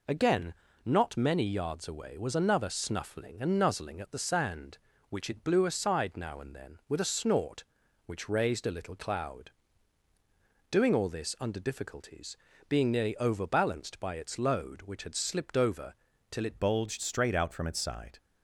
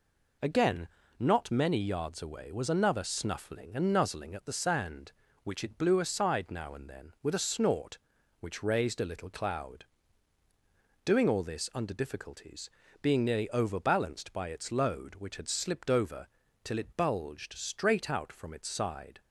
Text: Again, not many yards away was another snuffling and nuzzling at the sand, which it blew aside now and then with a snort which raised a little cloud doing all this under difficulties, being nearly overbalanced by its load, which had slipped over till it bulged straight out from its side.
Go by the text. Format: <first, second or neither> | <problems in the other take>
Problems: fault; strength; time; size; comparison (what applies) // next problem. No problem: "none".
second | pauses between "cloud" and "doing"; at 9.5 s; 1.2 s long; also in the second // pauses between "over" and "till"; at 15.9 s; 0.38 s long; also in the second // changes voice at "bulged"; from 16.5 s on; 1.6 s long